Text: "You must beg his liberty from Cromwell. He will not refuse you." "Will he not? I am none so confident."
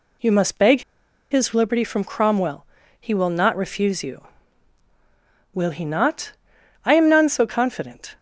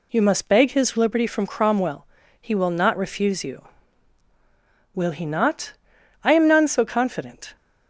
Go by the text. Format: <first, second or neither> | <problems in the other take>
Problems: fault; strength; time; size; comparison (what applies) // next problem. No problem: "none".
second | pauses between "beg" and "his"; noticeable; at 0.8 s; 0.49 s long